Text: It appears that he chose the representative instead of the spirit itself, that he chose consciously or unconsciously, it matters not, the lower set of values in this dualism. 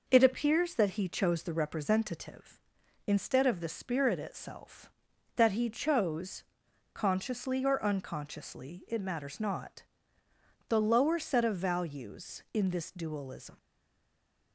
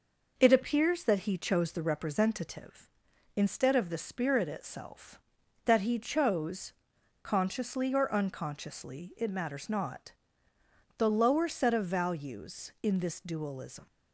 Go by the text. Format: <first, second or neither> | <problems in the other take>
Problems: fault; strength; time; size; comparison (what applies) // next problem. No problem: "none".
second | pauses between "chose" and "consciously"; noticeable; at 6.4 s; 0.48 s long; noticeable in the second // stays silent after the last word; from 13.5 s on; 1.0 s long